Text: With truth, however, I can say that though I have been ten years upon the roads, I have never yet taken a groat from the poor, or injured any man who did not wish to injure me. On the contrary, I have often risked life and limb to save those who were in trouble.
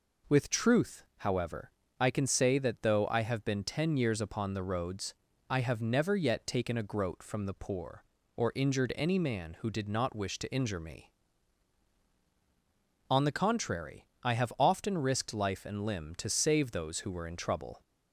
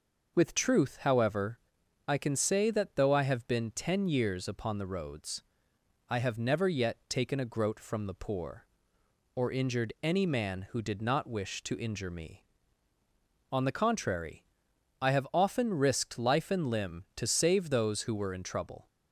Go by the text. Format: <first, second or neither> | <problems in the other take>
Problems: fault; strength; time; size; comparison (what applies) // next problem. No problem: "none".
neither | none